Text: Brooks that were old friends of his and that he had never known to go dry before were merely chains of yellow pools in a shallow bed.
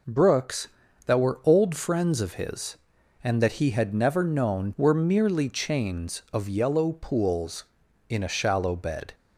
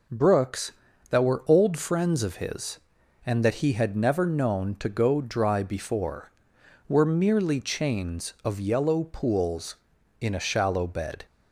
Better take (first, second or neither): second